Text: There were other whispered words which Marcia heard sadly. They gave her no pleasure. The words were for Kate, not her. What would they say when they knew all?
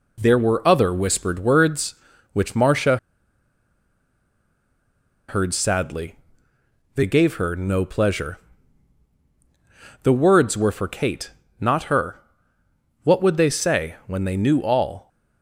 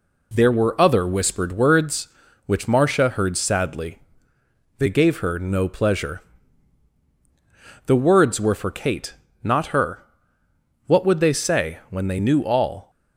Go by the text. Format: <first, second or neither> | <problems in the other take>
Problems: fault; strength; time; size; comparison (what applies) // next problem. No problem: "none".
second | pauses between "Marcia" and "heard"; strong; at 2.9 s; 2.3 s long